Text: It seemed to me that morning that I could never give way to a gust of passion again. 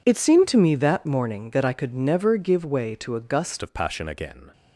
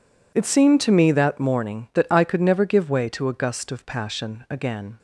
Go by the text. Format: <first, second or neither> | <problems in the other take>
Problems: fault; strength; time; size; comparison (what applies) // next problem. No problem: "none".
second | changes voice at "of"; from 3.6 s on; 0.8 s long